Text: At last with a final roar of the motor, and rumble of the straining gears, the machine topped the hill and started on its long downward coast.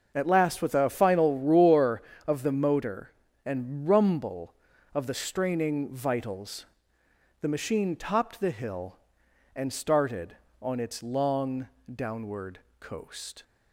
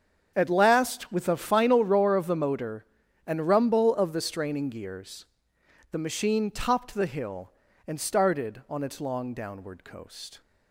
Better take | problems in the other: second | starts louder than the rest; until 1.1 s; 6.5 dB; strong in the second // says "vitals" for "gears"; at 5.8 s // pauses between "long" and "downward"; slight; at 11.6 s; 0.26 s long // pauses between "downward" and "coast"; slight; at 12.5 s; 0.20 s long

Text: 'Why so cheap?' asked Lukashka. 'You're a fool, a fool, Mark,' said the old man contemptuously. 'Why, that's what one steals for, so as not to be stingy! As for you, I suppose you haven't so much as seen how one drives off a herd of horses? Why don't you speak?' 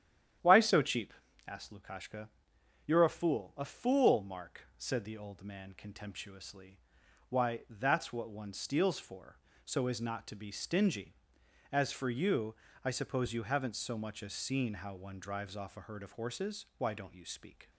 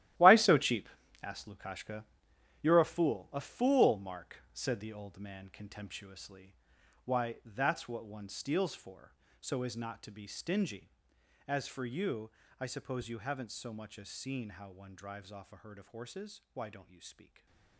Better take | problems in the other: first | gets quieter; strong; throughout; 11.5 dB // starts louder than the rest; strong; until 1.5 s; 14 dB; strong in the first // stays silent after the last word; slight; from 17.2 s on; 0.5 s long

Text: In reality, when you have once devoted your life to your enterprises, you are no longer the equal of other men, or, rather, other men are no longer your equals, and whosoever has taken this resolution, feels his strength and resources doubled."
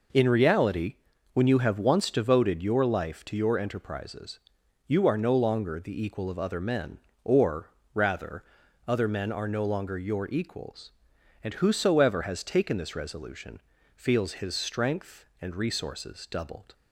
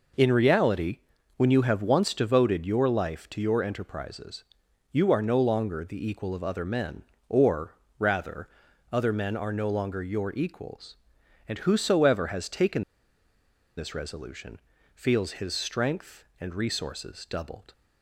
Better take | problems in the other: first | pauses between "taken" and "this"; noticeable; at 12.8 s; 0.94 s long

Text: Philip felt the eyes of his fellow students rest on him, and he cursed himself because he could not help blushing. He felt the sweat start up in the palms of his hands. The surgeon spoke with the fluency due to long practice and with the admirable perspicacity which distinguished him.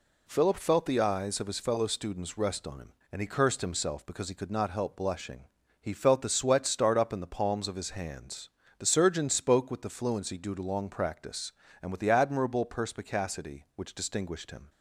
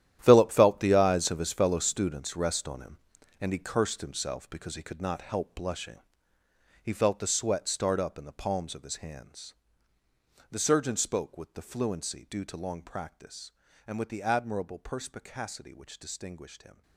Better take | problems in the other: first | gets quieter; strong; throughout; 14 dB

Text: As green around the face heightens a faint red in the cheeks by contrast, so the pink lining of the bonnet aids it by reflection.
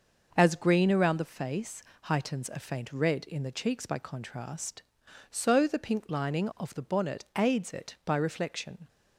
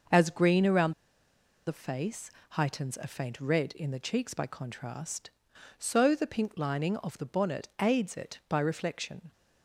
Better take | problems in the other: first | starts louder than the rest; noticeable; until 1.8 s; 6 dB; noticeable in the first // pauses between "around" and "the"; noticeable; at 0.9 s; 0.74 s long // pauses between "face" and "heightens"; slight; at 2.3 s; 0.20 s long; slight in the first

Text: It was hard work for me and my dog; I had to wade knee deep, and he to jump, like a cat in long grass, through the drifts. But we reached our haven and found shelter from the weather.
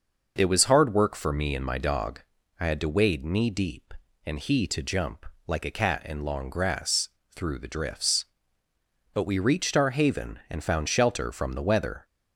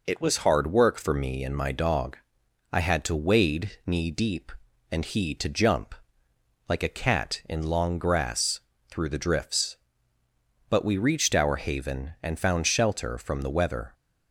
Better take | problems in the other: neither | none

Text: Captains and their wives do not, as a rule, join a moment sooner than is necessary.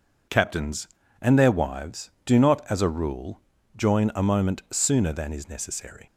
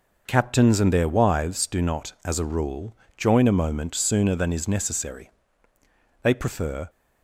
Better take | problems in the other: first | goes on to say "They prefer"; noticeable; from 6.2 s on; 0.66 s long

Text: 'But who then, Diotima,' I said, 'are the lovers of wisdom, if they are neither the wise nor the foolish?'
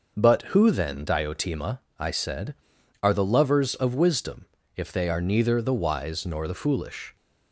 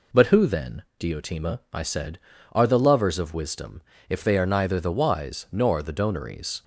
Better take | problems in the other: first | says "donaries" for "foolish"; at 5.9 s

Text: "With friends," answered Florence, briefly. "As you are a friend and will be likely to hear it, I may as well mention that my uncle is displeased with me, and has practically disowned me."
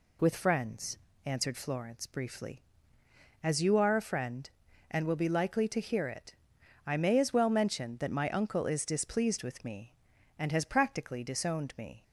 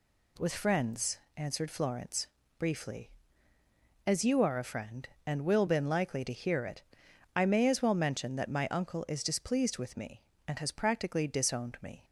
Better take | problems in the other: first | says "been" for "be"; at 5.6 s

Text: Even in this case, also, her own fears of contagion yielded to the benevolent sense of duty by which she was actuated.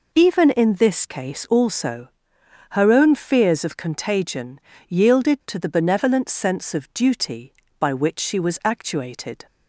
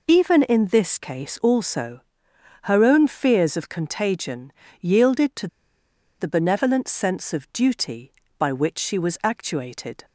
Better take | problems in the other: first | pauses between "contagion" and "yielded"; slight; at 4.5 s; 0.26 s long; slight in the first // pauses between "to" and "the"; noticeable; at 5.4 s; 0.73 s long

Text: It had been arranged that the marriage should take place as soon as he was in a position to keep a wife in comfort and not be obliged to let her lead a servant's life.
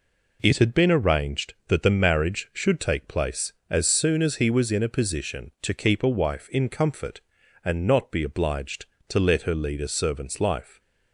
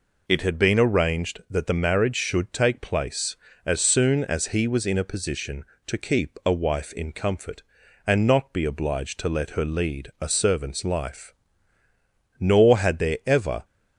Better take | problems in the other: first | goes on to say "Nor had there ever"; noticeable; from 12.3 s on; 1.2 s long

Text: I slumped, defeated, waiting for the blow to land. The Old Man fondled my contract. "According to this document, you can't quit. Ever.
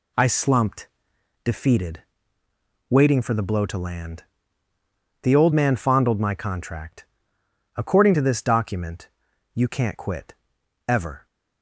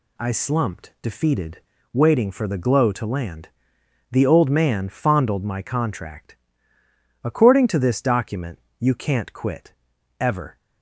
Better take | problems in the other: first | says "glow" for "blow"; at 2.5 s

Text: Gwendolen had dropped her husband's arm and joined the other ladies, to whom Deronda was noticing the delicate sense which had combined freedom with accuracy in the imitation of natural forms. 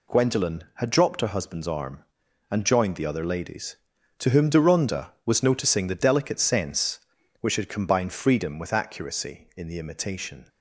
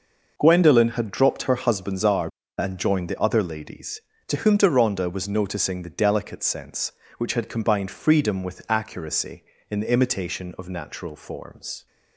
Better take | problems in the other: second | stops before "of natural forms"; at 10.4 s

